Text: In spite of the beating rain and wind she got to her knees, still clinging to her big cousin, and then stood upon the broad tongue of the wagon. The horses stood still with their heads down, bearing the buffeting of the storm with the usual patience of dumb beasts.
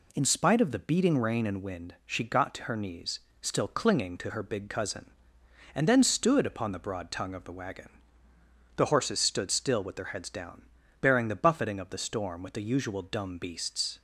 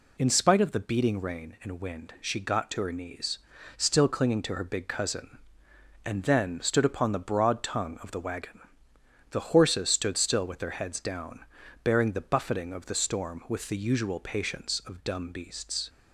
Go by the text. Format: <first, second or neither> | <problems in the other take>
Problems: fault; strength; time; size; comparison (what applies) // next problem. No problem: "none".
second | skips "patience of"; at 13.0 s